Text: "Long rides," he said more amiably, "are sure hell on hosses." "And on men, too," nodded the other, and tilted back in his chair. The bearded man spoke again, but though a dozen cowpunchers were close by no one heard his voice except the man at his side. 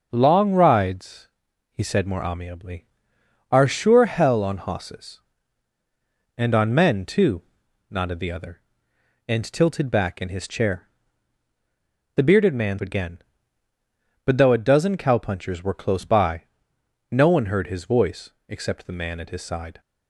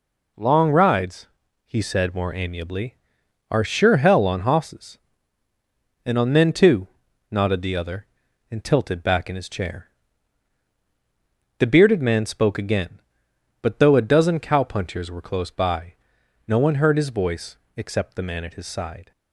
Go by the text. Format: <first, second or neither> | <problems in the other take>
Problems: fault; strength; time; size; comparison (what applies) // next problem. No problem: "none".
second | starts louder than the rest; noticeable; until 1.1 s; 6 dB // skips "spoke"; at 12.7 s // pauses between "by" and "no"; noticeable; at 16.4 s; 0.66 s long; noticeable in the second // pauses between "voice" and "except"; slight; at 18.3 s; 0.16 s long; slight in the second